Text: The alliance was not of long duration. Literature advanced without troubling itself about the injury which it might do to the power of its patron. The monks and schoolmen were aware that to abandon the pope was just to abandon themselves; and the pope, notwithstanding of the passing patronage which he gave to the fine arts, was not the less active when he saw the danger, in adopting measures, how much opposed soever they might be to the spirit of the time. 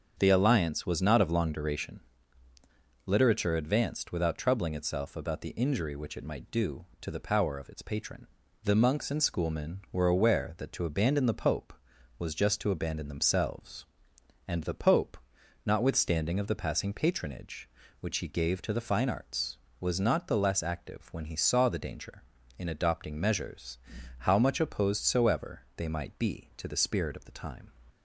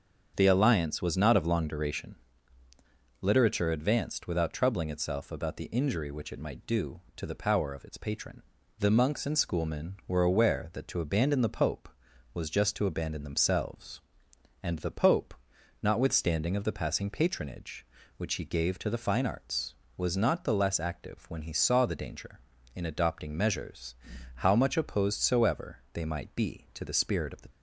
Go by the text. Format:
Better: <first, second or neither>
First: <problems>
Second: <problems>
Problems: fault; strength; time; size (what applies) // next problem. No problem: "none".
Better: first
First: starts louder than the rest; strong; until 1.2 s; 7.5 dB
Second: starts louder than the rest; strong; until 1.3 s; 7.5 dB // stops before "time"; at 27.5 s